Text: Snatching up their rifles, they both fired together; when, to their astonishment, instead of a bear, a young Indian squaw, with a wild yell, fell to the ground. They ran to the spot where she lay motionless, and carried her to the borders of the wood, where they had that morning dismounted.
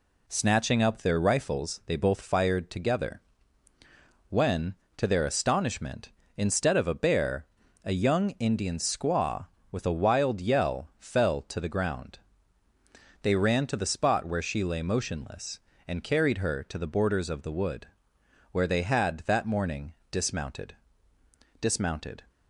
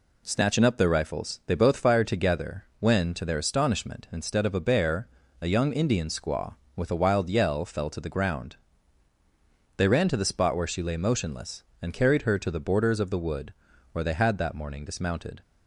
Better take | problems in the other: second | pauses between "morning" and "dismounted"; slight; at 19.9 s; 0.18 s long // says "dismounted" twice; at 21.5 s

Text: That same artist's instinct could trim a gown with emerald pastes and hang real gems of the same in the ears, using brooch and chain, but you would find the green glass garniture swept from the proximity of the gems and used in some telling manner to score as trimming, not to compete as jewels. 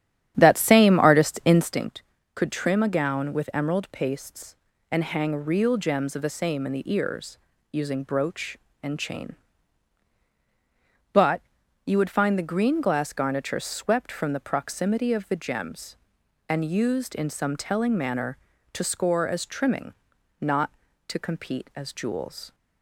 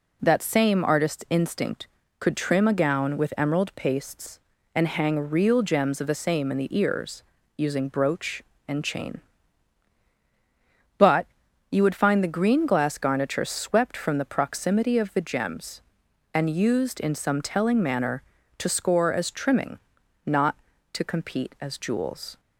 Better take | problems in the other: second | starts louder than the rest; strong; until 1.9 s; 10.5 dB // pauses between "but" and "you"; noticeable; at 11.4 s; 0.46 s long; noticeable in the second

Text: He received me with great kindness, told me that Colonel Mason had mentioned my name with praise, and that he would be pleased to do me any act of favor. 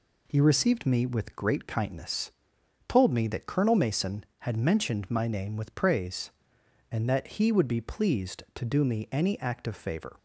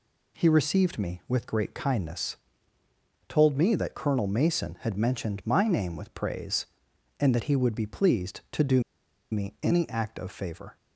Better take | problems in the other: first | pauses between "do" and "me"; noticeable; at 8.8 s; 0.49 s long

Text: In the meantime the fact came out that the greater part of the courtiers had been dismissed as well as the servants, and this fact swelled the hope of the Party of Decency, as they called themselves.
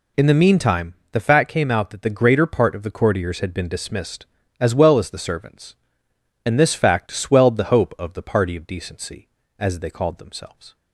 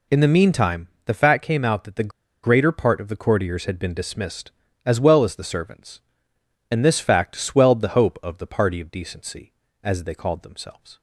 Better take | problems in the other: first | pauses between "meantime" and "the"; slight; at 0.8 s; 0.16 s long; slight in the first // pauses between "the" and "greater"; slight; at 2.1 s; 0.34 s long

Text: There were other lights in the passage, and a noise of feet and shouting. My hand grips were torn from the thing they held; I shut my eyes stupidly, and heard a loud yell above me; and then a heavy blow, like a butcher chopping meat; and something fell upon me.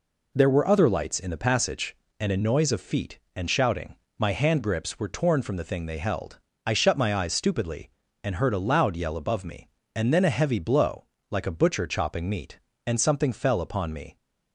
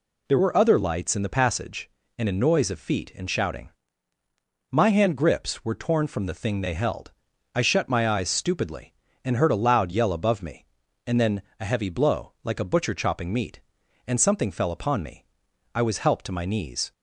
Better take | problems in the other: first | pauses between "then" and "a"; slight; at 11.4 s; 0.18 s long // goes on to say "I was helped to my knees"; noticeable; from 15.7 s on; 1.1 s long

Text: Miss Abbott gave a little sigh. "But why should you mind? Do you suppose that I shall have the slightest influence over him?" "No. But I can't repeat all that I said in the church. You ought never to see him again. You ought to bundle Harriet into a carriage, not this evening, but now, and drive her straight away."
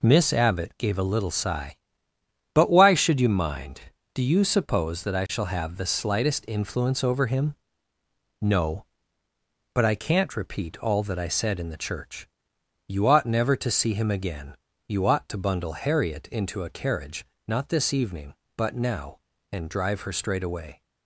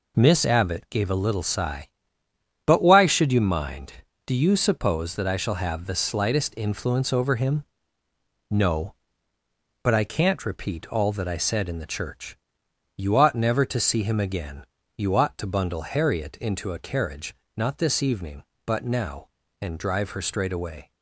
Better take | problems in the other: neither | none

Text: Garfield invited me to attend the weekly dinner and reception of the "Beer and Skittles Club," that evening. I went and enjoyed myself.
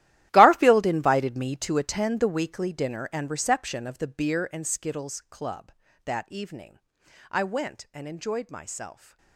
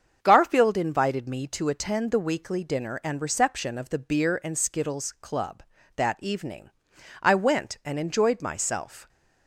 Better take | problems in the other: second | gets quieter; strong; throughout; 16 dB // starts louder than the rest; strong; until 1.3 s; 14 dB; also in the second

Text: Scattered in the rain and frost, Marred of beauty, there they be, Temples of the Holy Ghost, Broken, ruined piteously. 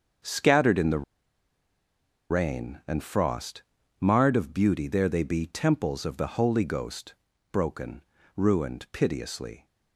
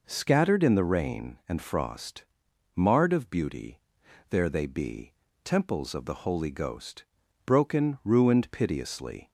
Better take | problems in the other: second | starts louder than the rest; until 2.5 s; 7 dB // pauses between "the" and "rain"; strong; at 1.0 s; 1.2 s long

